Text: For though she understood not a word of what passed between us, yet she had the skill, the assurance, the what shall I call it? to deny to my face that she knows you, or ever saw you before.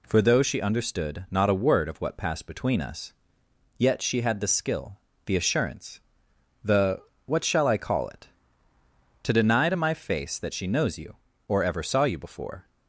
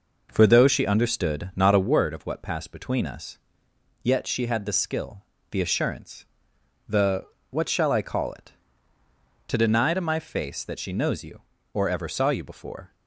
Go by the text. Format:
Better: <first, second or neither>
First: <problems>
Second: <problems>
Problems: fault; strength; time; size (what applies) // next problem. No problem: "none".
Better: first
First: pauses between "the" and "what"; slight; at 7.0 s; 0.24 s long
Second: starts louder than the rest; noticeable; until 2.0 s; 5 dB // pauses between "the" and "what"; slight; at 7.2 s; 0.24 s long